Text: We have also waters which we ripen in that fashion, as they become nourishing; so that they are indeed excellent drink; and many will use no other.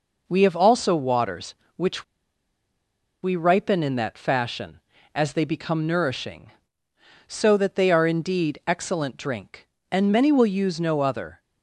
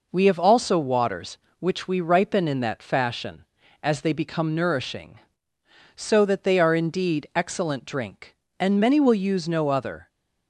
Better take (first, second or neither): second